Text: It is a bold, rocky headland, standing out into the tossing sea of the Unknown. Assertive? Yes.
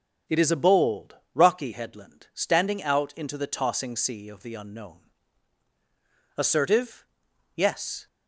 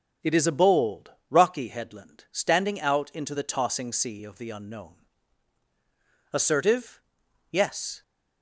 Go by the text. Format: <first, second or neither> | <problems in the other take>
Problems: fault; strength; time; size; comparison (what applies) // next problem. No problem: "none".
neither | starts louder than the rest; the same in both